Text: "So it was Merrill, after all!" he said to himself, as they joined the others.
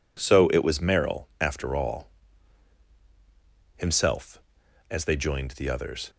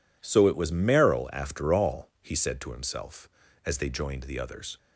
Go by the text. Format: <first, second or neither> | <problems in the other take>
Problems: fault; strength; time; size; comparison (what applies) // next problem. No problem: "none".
second | skips "he said to"; at 2.9 s